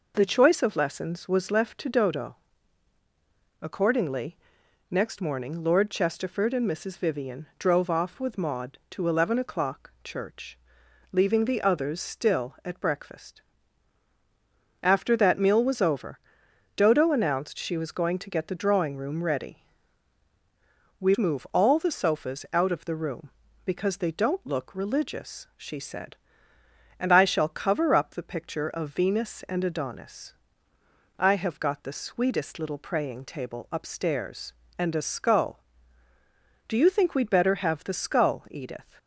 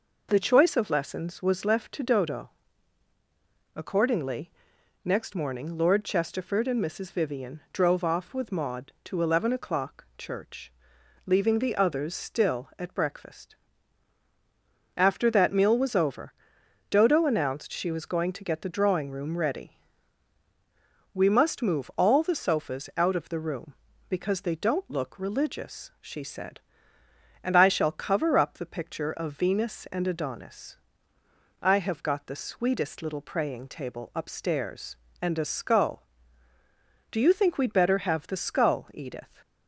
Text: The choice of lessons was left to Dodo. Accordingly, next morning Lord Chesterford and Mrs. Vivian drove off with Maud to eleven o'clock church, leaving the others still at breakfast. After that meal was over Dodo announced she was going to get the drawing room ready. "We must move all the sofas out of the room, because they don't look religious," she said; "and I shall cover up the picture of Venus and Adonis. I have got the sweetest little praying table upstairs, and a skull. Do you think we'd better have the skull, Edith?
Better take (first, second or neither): second